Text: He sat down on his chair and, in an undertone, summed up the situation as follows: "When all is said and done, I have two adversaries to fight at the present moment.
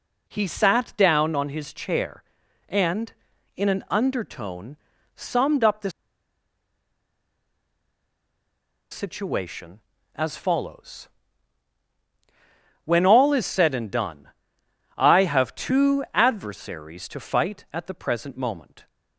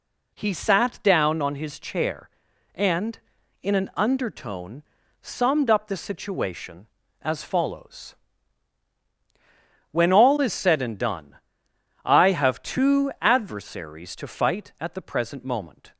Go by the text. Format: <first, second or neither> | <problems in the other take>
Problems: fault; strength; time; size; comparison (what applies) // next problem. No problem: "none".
second | pauses between "the" and "situation"; strong; at 5.8 s; 3.0 s long